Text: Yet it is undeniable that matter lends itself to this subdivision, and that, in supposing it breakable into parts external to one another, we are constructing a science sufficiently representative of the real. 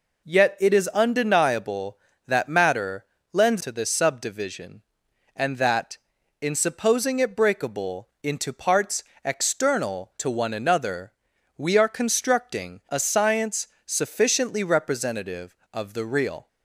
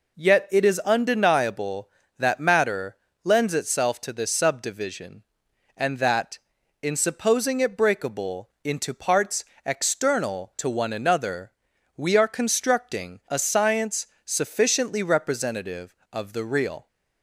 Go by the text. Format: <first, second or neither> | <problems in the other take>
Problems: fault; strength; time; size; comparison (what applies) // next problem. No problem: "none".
second | pauses between "matter" and "lends"; slight; at 3.0 s; 0.28 s long; slight in the second // skips "itself"; at 3.6 s // pauses between "parts" and "external"; slight; at 9.0 s; 0.20 s long; slight in the second // pauses between "science" and "sufficiently"; slight; at 13.6 s; 0.18 s long; slight in the second